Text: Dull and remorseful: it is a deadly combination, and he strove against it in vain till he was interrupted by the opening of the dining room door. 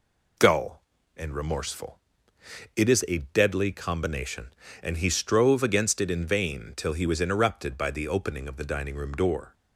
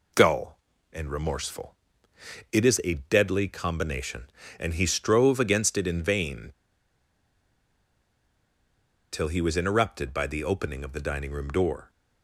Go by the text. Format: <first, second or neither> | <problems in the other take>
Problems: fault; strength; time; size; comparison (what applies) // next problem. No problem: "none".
first | pauses between "vain" and "till"; strong; at 6.5 s; 2.6 s long